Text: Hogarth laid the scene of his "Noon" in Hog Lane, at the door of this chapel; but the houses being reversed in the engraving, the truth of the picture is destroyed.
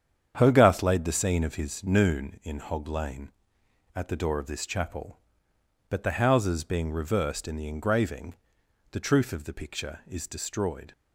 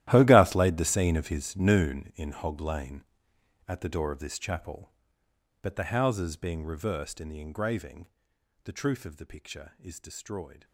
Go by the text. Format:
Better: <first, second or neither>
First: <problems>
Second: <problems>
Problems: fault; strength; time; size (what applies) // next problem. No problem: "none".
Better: first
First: starts louder than the rest; strong; until 1.3 s; 8.5 dB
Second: gets quieter; strong; throughout; 16 dB // starts louder than the rest; strong; until 1.0 s; 13.5 dB